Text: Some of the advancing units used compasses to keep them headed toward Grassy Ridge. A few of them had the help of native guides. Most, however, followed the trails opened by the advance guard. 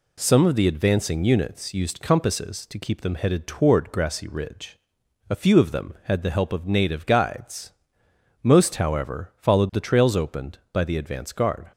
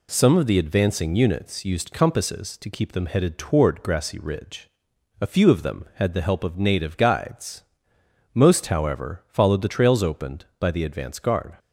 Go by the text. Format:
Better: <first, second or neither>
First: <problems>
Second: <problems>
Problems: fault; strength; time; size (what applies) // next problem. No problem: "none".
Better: neither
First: none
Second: none